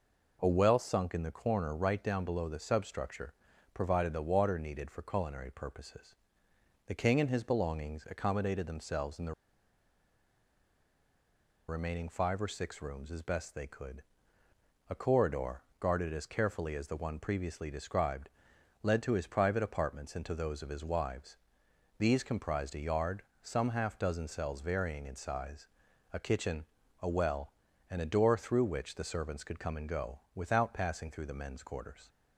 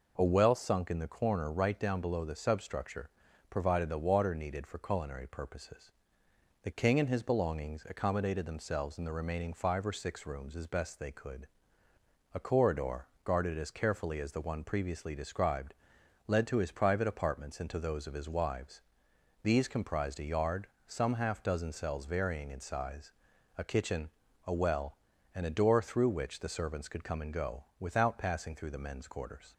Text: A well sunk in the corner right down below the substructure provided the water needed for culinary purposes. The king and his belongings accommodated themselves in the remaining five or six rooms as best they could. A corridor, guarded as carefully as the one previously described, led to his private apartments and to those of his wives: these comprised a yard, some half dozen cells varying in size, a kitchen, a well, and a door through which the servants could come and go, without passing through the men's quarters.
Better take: second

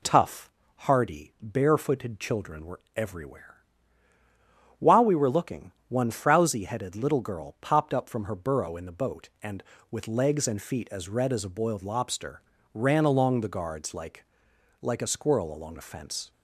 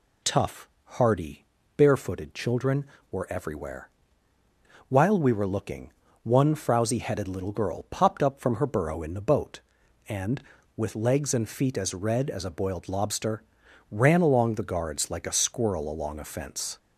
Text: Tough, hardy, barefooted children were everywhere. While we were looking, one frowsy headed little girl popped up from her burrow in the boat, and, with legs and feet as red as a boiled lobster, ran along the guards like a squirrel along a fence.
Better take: second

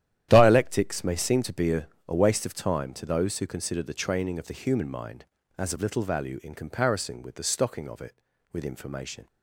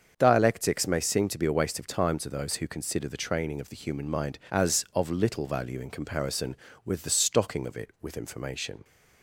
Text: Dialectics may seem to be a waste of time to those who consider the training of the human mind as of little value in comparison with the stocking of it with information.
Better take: second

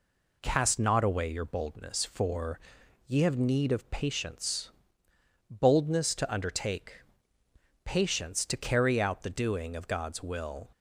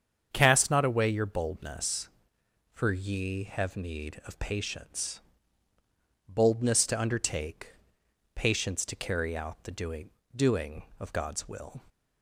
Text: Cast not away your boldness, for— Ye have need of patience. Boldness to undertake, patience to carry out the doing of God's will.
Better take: first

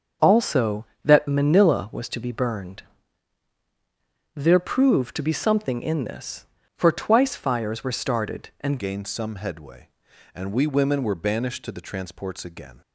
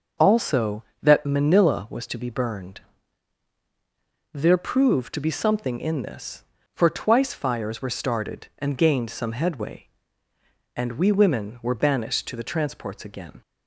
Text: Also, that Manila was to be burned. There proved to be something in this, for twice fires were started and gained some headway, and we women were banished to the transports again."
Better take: second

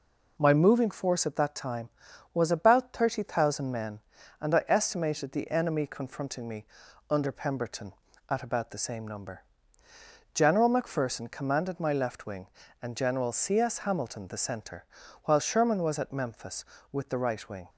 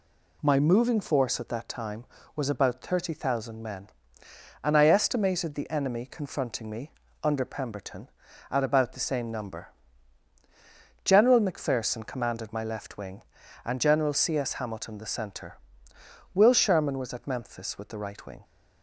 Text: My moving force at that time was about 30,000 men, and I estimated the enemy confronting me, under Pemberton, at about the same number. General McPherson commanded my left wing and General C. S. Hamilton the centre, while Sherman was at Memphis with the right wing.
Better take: first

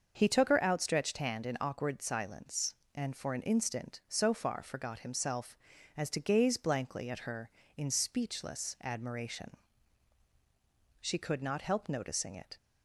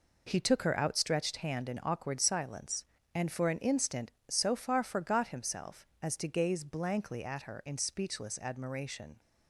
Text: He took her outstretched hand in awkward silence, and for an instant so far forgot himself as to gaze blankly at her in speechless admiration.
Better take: second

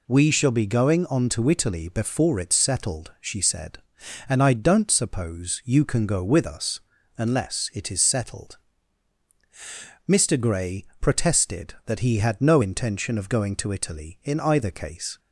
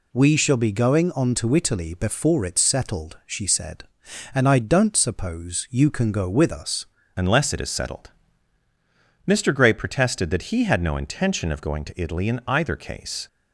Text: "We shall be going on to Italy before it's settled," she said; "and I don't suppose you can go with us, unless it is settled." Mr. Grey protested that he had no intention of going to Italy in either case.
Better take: first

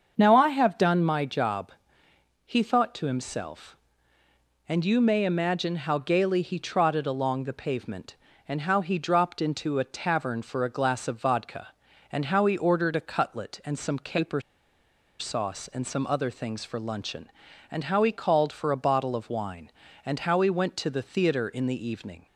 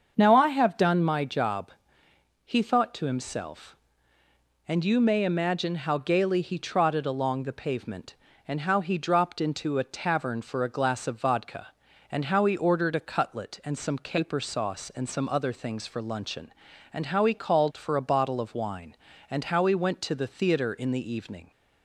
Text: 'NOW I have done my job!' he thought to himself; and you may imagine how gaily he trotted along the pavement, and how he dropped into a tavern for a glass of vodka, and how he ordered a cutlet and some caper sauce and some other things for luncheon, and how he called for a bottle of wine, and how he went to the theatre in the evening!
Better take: second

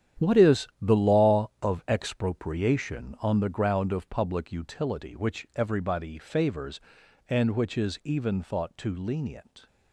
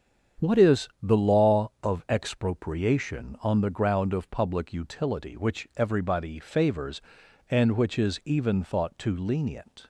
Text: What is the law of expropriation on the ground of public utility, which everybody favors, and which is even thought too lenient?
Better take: second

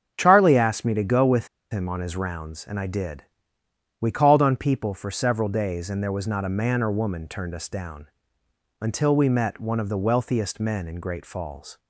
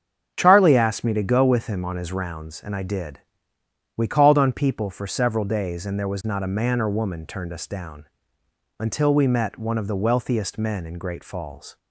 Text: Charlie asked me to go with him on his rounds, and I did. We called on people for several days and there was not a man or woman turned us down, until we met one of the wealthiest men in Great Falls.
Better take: second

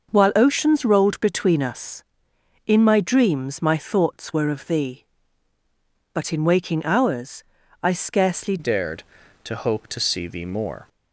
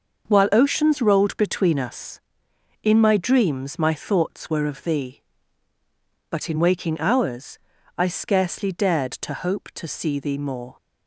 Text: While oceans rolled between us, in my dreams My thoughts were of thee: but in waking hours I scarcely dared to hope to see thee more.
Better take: second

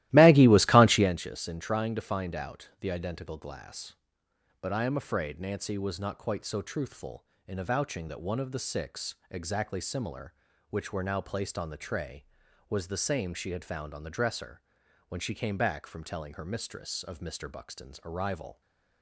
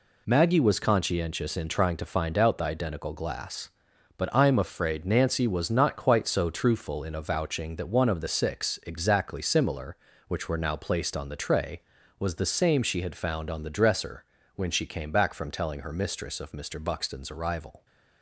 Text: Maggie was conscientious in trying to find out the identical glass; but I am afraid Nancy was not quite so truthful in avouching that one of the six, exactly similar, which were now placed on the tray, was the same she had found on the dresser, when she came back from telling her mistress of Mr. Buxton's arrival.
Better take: second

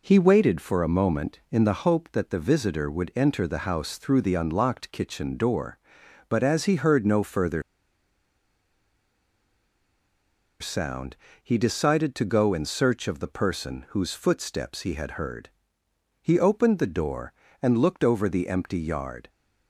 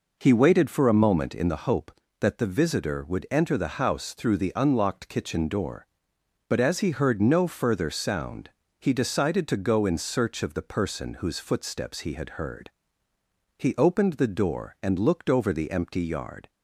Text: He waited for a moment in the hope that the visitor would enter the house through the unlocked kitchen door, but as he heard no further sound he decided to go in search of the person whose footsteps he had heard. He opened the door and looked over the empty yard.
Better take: second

